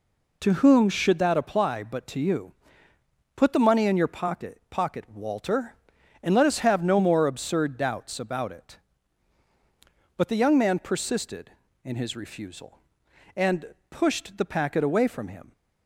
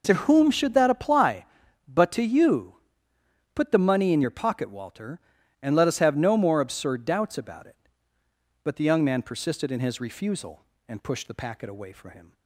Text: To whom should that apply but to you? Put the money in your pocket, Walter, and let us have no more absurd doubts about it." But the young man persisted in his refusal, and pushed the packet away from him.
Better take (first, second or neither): second